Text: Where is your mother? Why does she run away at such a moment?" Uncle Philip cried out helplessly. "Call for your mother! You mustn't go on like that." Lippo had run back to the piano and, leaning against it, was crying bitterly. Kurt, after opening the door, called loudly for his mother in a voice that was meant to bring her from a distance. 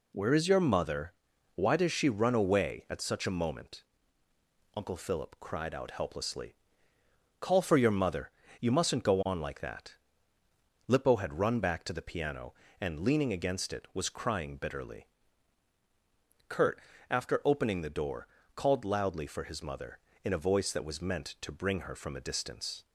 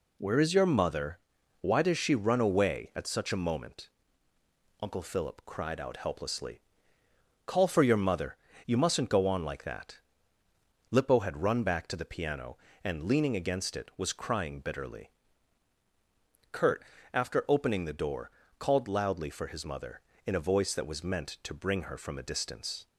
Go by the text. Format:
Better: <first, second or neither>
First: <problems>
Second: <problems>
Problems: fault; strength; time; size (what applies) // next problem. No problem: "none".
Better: neither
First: none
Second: none